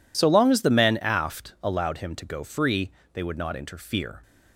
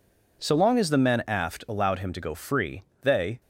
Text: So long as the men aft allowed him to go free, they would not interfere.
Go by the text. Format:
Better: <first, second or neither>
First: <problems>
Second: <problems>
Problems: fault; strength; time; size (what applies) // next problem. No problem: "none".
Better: first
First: none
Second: stops before "would not interfere"; at 3.4 s